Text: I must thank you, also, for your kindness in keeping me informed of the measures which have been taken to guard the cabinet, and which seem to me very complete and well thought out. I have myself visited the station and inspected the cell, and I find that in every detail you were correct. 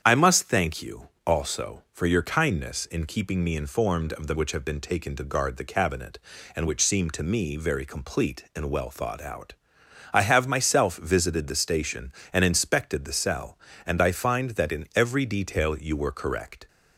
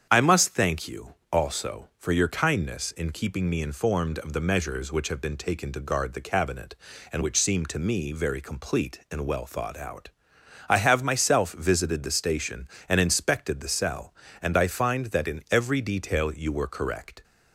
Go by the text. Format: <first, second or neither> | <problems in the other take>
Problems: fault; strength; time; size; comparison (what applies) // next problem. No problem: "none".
second | starts louder than the rest; strong; until 1.0 s; 8.5 dB; strong in the second // skips "measures"; at 4.3 s